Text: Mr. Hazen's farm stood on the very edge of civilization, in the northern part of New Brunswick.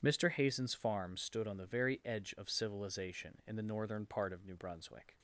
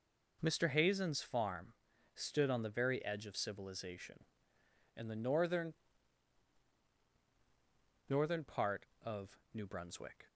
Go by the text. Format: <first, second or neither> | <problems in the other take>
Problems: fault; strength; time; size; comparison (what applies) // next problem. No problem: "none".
first | pauses between "farm" and "stood"; at 1.7 s; 0.40 s long // says "northern" twice; at 8.0 s // pauses between "of" and "New"; slight; at 9.3 s; 0.16 s long